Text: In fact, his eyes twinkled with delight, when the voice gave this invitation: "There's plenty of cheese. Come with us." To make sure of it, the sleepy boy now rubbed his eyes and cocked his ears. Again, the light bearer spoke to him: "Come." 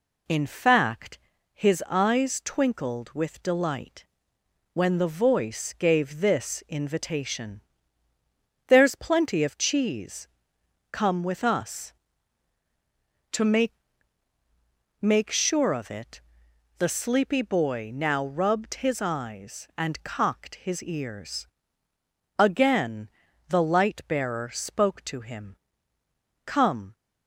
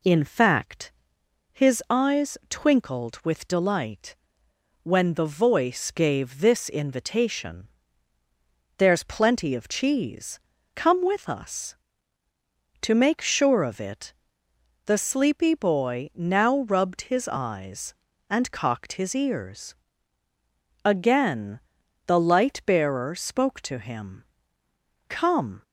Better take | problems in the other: second | says "make" twice; at 14.9 s

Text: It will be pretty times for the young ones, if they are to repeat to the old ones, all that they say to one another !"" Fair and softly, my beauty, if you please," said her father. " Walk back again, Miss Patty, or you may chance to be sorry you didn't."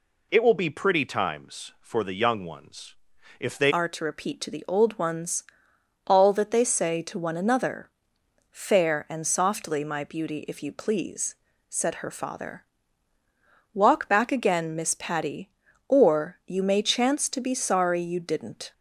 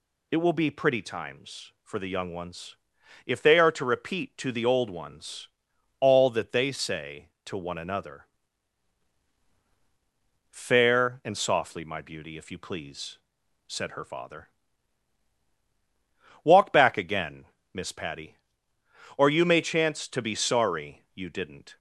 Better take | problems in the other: second | changes voice at "are"; from 3.6 s on; 15.1 s long

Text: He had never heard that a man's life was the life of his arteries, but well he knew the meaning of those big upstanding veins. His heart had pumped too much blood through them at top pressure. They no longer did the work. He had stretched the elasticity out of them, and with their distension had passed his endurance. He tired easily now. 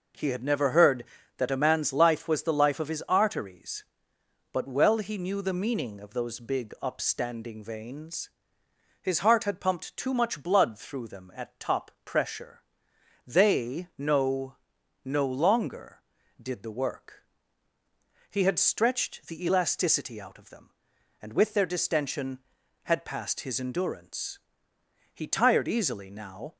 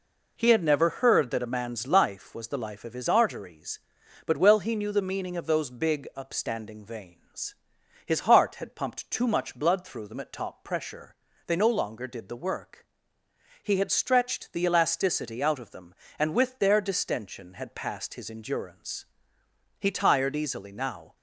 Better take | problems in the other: second | says "no" twice; at 15.0 s

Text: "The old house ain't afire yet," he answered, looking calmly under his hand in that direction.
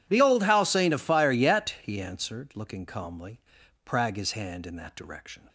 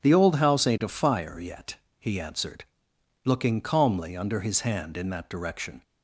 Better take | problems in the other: second | says "prag" for "under"; at 3.8 s

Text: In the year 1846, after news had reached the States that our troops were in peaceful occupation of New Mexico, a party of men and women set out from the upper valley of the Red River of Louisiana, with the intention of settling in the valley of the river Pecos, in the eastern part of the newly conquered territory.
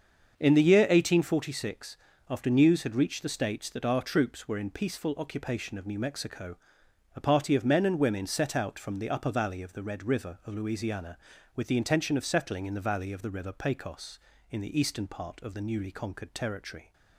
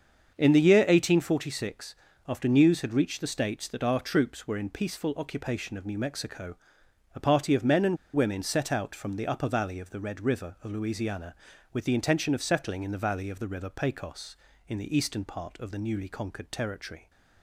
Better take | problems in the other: first | starts louder than the rest; until 1.3 s; 7 dB; also in the first // pauses between "and" and "women"; slight; at 7.9 s; 0.19 s long

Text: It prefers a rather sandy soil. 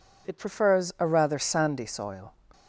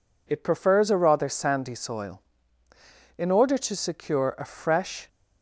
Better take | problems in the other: first | goes on to say "In order to secure a fresh"; strong; from 3.1 s on; 1.9 s long

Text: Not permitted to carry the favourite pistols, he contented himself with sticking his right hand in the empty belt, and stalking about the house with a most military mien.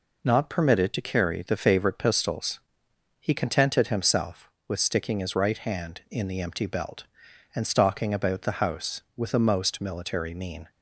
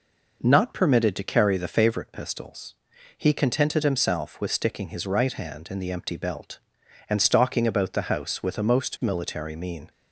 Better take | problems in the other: neither | none

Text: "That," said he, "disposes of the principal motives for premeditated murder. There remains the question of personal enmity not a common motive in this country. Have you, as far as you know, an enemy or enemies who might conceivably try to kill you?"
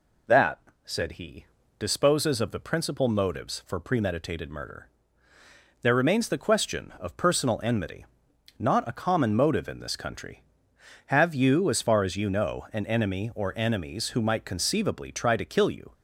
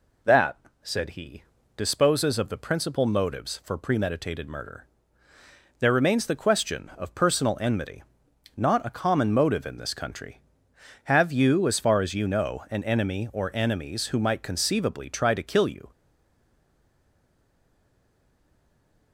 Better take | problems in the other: first | pauses between "enmity" and "not"; noticeable; at 8.0 s; 0.52 s long; noticeable in the first // stays silent after the last word; strong; from 15.9 s on; 3.2 s long

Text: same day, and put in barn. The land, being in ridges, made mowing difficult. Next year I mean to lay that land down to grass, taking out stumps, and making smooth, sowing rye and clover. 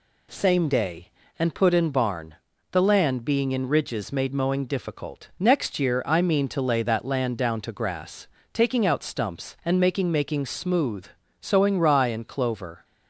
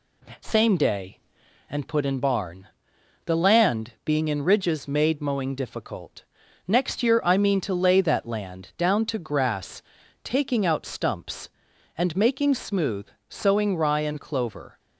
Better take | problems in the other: second | says "making" twice; at 10.1 s

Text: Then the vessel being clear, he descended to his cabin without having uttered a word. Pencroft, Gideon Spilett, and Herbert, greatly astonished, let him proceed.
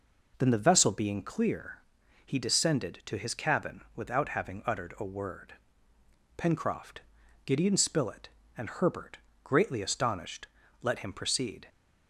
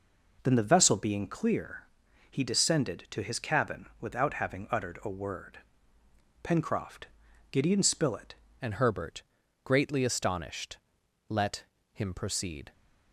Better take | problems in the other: first | changes voice at "and"; from 8.6 s on; 4.1 s long // pauses between "let" and "him"; slight; at 11.6 s; 0.28 s long

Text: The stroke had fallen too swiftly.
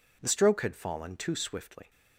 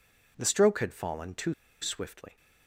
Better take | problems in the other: first | pauses between "too" and "swiftly"; slight; at 1.5 s; 0.28 s long

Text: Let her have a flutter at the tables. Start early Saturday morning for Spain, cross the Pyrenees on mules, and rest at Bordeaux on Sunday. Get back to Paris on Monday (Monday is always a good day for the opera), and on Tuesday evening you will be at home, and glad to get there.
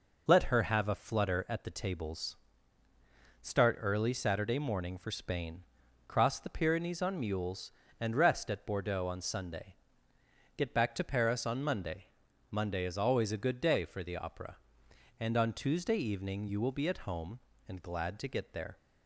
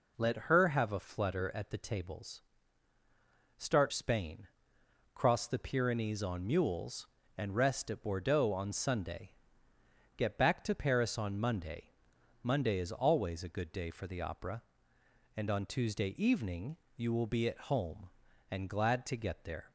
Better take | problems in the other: first | skips "early Saturday morning for"; at 3.9 s // pauses between "evening" and "you"; slight; at 16.7 s; 0.18 s long

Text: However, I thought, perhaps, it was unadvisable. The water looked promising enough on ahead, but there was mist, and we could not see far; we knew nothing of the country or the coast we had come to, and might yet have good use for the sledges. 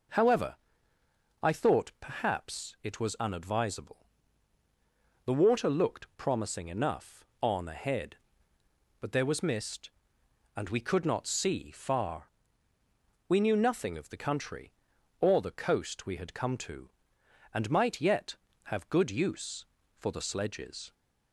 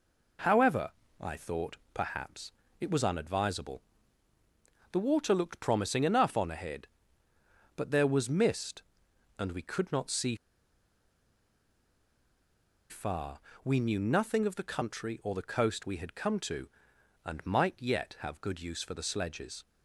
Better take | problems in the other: first | pauses between "see" and "far"; strong; at 10.3 s; 2.5 s long

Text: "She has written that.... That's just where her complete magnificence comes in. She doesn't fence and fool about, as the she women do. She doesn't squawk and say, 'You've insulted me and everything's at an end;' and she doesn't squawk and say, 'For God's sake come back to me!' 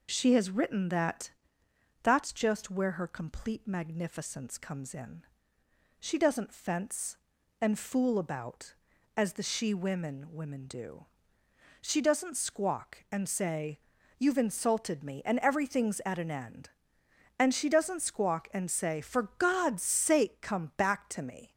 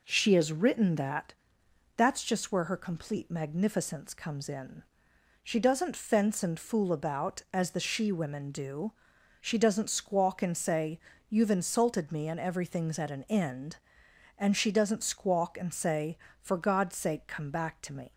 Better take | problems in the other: second | says "women" twice; at 10.3 s

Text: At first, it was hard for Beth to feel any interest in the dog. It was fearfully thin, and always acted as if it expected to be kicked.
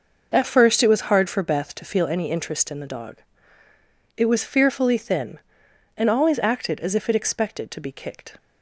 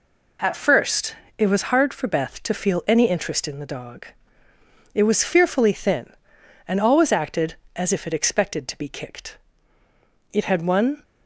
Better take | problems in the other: first | goes on to say "It had one"; noticeable; from 10.3 s on; 0.70 s long

